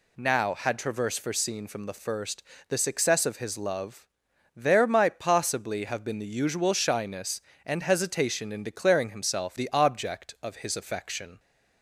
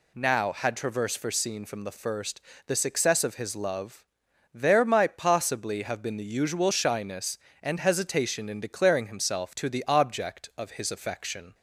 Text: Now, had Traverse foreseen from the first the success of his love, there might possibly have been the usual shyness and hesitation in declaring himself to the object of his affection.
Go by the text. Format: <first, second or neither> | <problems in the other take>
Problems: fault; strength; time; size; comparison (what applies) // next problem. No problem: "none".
second | pauses between "first" and "the"; slight; at 2.4 s; 0.28 s long; slight in the second // skips "to"; at 9.5 s